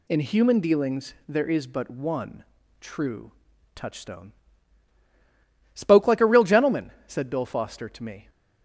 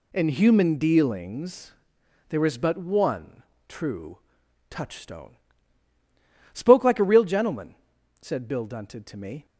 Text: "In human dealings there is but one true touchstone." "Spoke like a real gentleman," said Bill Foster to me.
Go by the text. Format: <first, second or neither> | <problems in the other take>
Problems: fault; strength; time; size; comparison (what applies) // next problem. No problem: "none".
first | pauses between "dealings" and "there"; noticeable; at 1.7 s; 0.56 s long // pauses between "one" and "true"; slight; at 3.4 s; 0.24 s long; slight in the first // pauses between "true" and "touchstone"; noticeable; at 4.1 s; 0.54 s long; also in the first // says "Dunted" for "Foster"; at 8.6 s